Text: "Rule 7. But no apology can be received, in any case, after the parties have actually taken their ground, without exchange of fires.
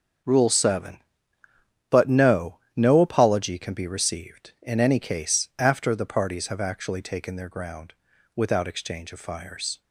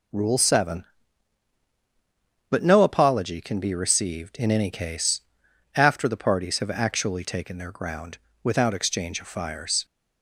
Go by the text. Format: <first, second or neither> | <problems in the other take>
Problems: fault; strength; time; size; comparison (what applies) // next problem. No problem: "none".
second | starts louder than the rest; until 2.1 s; 6.5 dB // says "no" twice; at 2.7 s